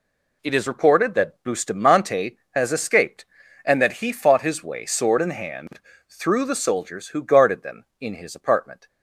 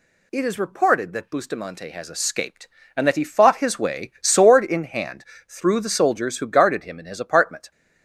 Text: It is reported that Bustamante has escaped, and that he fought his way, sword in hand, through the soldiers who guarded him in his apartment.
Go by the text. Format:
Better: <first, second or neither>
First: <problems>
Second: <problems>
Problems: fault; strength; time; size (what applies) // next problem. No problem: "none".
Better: second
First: says "them" for "him"; at 7.6 s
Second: none